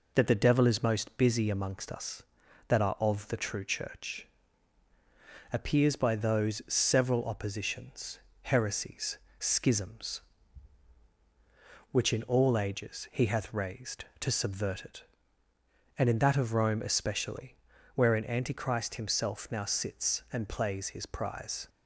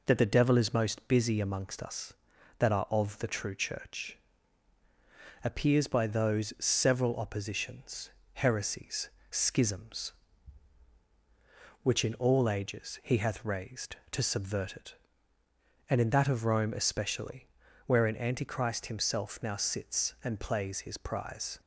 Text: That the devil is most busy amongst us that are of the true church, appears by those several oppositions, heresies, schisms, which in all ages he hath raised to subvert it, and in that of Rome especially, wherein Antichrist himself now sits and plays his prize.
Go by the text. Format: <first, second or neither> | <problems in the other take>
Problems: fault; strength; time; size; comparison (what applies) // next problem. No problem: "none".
neither | none